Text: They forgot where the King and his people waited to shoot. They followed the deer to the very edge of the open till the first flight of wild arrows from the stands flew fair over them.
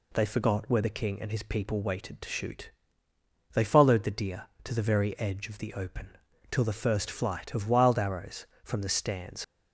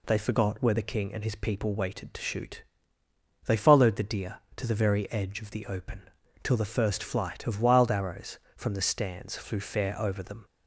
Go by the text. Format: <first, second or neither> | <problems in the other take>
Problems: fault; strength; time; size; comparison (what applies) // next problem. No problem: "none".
second | pauses between "open" and "till"; at 6.0 s; 0.42 s long; also in the second // stops before "flew fair over them"; at 9.4 s